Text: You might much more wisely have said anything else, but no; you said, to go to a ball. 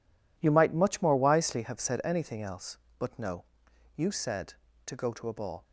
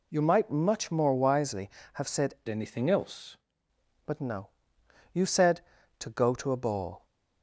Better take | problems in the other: first | changes voice from "anything" to "else"; from 2.4 to 3.3 s; 0.9 s long

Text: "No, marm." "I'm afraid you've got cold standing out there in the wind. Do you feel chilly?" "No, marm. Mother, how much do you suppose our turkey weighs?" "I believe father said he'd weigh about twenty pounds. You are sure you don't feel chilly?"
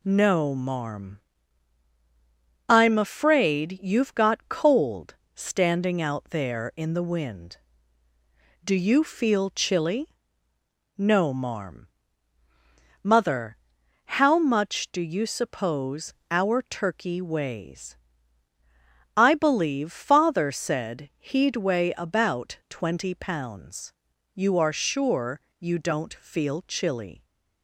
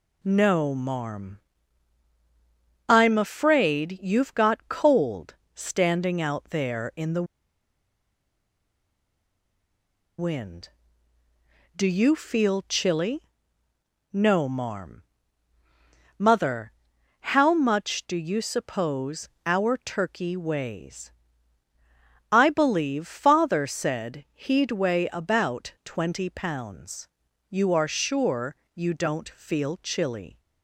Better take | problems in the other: first | pauses between "cold" and "standing"; slight; at 5.3 s; 0.22 s long; slight in the first // pauses between "the" and "wind"; strong; at 7.2 s; 2.9 s long // pauses between "suppose" and "our"; slight; at 19.2 s; 0.18 s long; slight in the first // pauses between "sure" and "you"; slight; at 28.5 s; 0.18 s long; slight in the first

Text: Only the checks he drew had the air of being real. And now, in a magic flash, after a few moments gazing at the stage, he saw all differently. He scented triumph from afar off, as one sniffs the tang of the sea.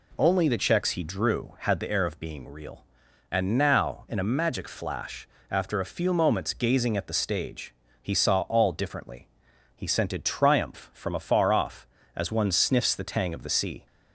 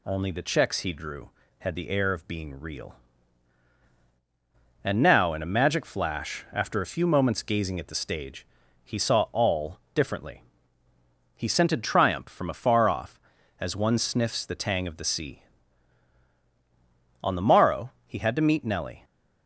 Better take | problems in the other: first | pauses between "all" and "differently"; slight; at 9.7 s; 0.16 s long // goes on to say "On the morrow he had to meet Nellie"; strong; from 17.2 s on; 1.8 s long

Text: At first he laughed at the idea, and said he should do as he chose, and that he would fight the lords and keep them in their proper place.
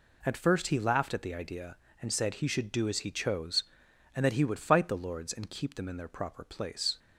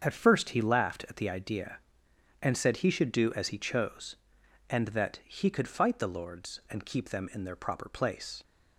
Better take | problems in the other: first | starts louder than the rest; strong; until 1.0 s; 7 dB // says "could" for "would"; at 5.4 s

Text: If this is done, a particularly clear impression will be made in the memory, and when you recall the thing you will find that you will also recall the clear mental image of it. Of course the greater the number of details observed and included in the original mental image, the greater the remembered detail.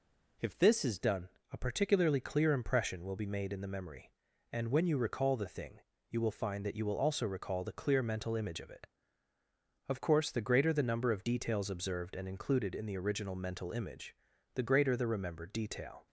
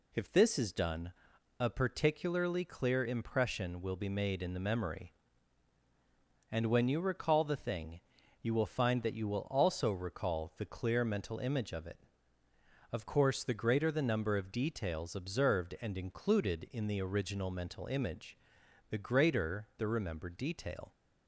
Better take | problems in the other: second | changes voice at "done"; from 1.0 s on; 15.0 s long // pauses between "thing" and "you"; slight; at 5.8 s; 0.30 s long; also in the second

